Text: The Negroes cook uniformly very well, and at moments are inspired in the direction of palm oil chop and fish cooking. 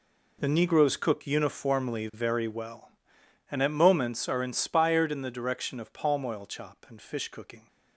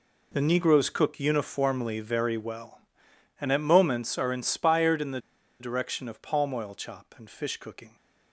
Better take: first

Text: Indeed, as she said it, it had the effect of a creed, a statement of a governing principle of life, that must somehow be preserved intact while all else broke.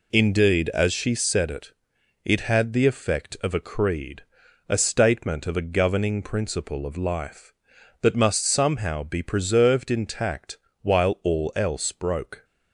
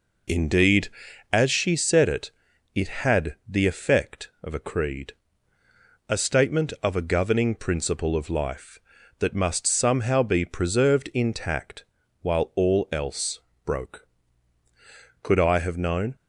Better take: first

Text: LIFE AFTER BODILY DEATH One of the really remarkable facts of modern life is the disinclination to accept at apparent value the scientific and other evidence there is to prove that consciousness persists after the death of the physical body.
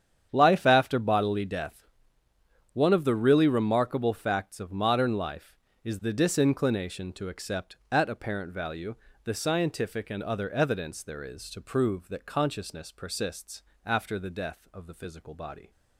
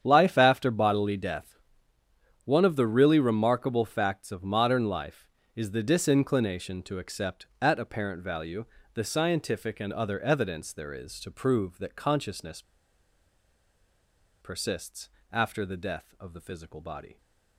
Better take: first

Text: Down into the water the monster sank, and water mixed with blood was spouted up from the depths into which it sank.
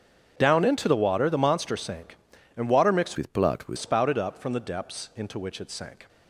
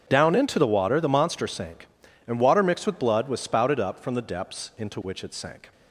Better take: second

